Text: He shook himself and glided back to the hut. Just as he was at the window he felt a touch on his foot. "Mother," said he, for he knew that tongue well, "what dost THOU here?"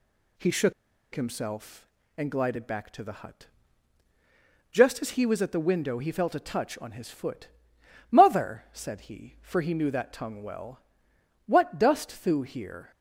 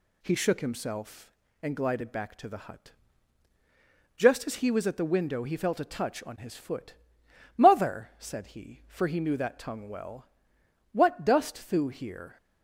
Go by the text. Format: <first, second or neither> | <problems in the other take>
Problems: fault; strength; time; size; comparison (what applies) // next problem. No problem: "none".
second | pauses between "shook" and "himself"; at 0.7 s; 0.41 s long